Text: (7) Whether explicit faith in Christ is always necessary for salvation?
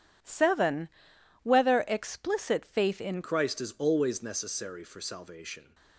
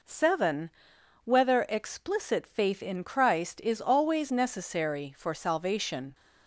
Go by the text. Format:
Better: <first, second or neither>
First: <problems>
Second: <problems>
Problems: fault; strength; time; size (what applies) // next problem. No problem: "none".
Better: second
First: changes voice at "Christ"; from 3.2 s on; 2.5 s long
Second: none